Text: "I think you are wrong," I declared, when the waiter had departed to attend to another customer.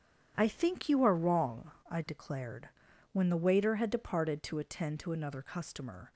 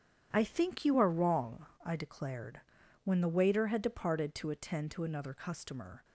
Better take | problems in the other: neither | starts louder than the rest; strong; the same in both

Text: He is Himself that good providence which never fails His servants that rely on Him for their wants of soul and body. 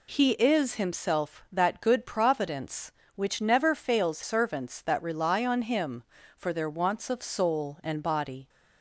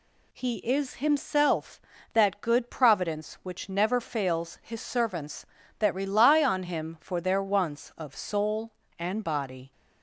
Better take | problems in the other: second | skips "His"; at 4.2 s

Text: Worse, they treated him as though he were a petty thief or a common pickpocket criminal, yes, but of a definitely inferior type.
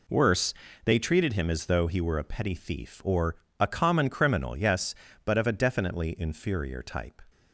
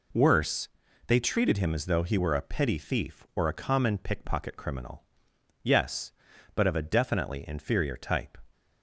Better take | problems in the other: second | pauses between "or" and "a"; slight; at 3.3 s; 0.24 s long // skips "pickpocket"; at 4.0 s

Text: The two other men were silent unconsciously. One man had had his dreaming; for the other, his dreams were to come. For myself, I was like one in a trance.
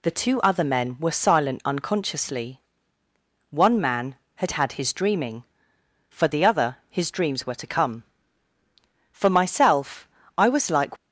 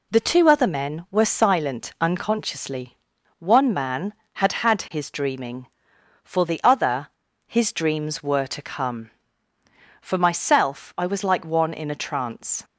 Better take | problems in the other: second | stops before "one in a trance"; at 10.9 s

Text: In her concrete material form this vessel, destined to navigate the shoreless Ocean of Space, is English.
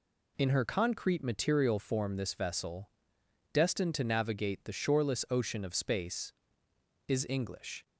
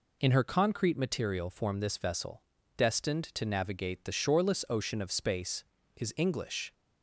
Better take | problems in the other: neither | none

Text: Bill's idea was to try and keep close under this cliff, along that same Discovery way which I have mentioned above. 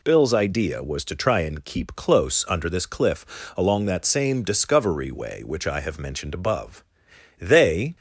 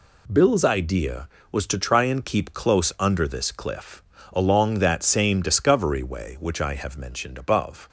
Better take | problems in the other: second | goes on to say "They"; from 7.3 s on; 0.56 s long

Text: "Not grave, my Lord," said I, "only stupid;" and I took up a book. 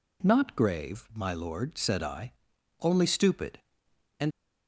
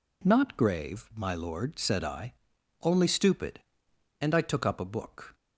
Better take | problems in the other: second | stops before "I took up a book"; at 4.3 s

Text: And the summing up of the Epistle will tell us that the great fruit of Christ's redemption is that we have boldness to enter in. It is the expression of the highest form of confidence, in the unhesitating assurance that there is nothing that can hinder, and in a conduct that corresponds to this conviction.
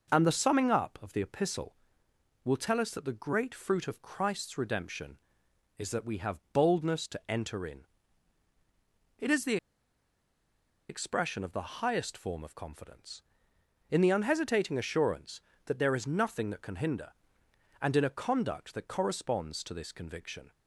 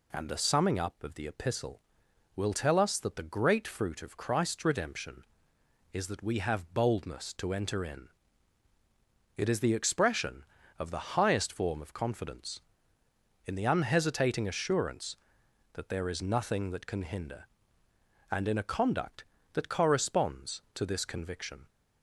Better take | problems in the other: second | pauses between "the" and "expression"; strong; at 9.5 s; 1.3 s long

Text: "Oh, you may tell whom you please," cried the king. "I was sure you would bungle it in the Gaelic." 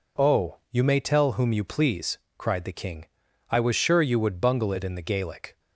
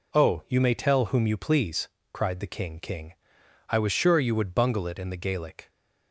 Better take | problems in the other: first | says "king" twice; at 2.7 s

